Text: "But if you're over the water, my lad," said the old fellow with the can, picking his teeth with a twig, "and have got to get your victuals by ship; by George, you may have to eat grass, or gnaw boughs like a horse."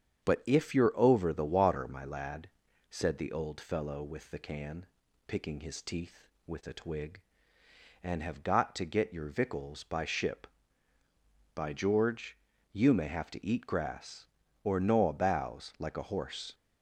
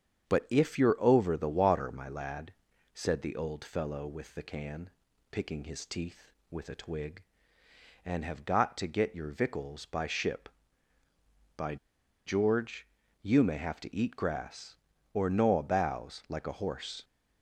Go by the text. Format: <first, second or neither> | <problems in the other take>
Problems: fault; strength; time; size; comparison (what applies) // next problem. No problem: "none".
first | starts louder than the rest; strong; until 1.3 s; 8 dB; strong in the first // pauses between "by" and "George"; noticeable; at 11.7 s; 0.50 s long